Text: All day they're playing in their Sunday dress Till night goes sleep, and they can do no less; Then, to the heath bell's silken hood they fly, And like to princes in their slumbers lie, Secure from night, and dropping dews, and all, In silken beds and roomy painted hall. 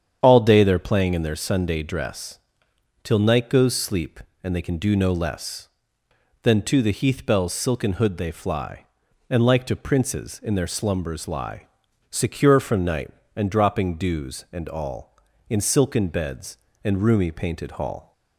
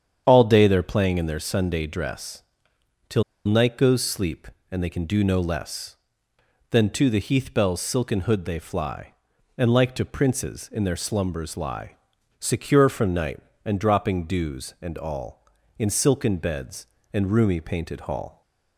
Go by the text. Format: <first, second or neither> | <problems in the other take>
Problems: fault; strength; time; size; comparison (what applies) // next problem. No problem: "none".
first | starts louder than the rest; strong; until 1.2 s; 8.5 dB; strong in the first // pauses between "dress" and "Till"; noticeable; at 2.4 s; 0.66 s long; noticeable in the first // pauses between "Till" and "night"; slight; at 3.2 s; 0.24 s long